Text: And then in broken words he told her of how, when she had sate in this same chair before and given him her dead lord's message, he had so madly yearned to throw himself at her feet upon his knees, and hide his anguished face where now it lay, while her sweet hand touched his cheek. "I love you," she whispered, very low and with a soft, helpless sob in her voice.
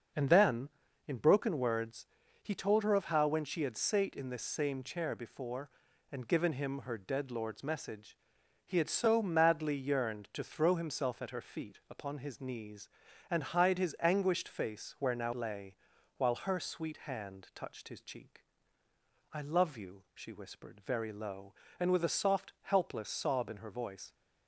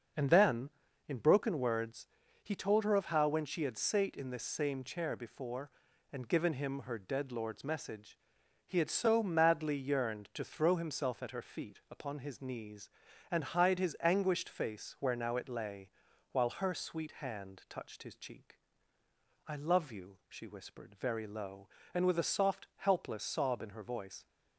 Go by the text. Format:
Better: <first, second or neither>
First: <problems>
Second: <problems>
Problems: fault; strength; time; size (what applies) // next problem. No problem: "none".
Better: second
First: starts louder than the rest; noticeable; until 1.5 s; 6 dB // pauses between "words" and "he"; slight; at 2.0 s; 0.36 s long // skips "it"; at 15.3 s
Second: starts louder than the rest; noticeable; until 1.5 s; 6 dB // pauses between "words" and "he"; slight; at 2.0 s; 0.36 s long